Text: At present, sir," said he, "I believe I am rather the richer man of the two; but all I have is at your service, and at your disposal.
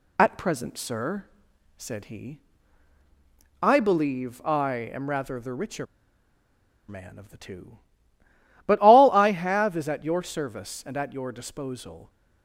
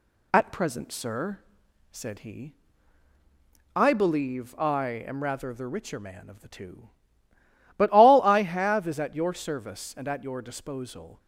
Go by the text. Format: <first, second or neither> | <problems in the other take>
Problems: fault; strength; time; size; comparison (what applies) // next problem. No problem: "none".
second | pauses between "richer" and "man"; at 5.8 s; 1.0 s long